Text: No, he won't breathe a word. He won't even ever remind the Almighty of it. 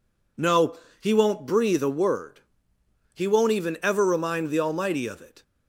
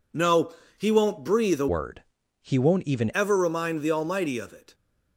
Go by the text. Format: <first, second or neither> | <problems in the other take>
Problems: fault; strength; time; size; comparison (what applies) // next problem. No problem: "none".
first | changes voice from "word" to "even"; from 1.6 to 3.1 s; 1.5 s long